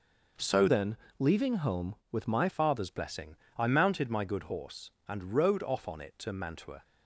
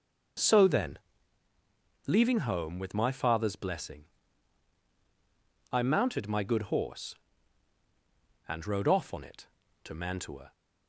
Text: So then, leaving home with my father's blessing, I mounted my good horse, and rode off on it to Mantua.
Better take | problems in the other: second | changes voice from "then" to "my"; from 0.6 to 2.4 s; 1.8 s long

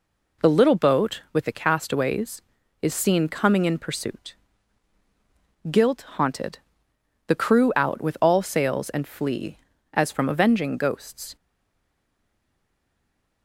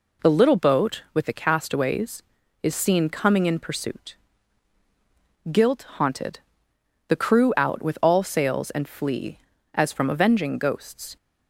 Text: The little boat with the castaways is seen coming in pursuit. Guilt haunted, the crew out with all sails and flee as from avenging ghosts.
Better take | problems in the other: second | stays silent after the last word; noticeable; from 11.3 s on; 2.1 s long

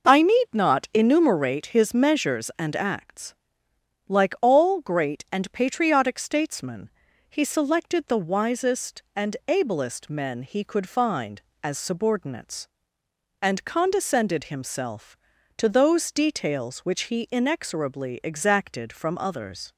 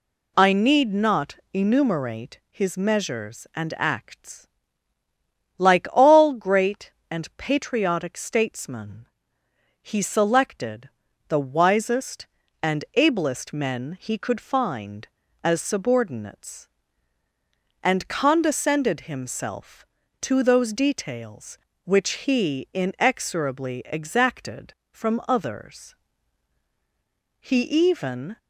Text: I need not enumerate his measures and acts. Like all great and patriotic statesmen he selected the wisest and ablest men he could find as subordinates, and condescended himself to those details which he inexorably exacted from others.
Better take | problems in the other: first | pauses between "not" and "enumerate"; slight; at 1.3 s; 0.16 s long // pauses between "statesmen" and "he"; noticeable; at 9.0 s; 0.80 s long; also in the first // pauses between "selected" and "the"; at 10.8 s; 0.40 s long // goes on to say "He even"; noticeable; from 27.3 s on; 0.98 s long

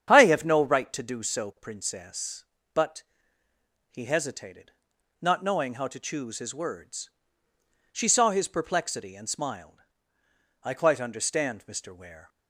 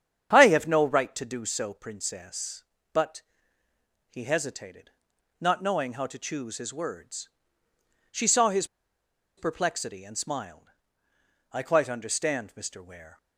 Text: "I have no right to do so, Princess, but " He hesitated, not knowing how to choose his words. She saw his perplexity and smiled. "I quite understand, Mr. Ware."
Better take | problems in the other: first | starts louder than the rest; strong; until 1.3 s; 8.5 dB; strong in the first // pauses between "his" and "perplexity"; noticeable; at 8.6 s; 0.71 s long

